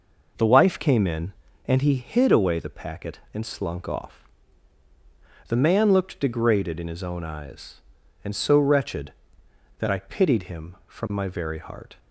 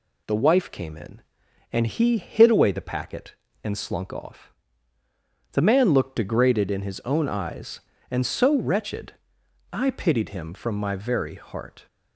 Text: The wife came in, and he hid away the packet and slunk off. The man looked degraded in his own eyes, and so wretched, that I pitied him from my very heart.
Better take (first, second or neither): first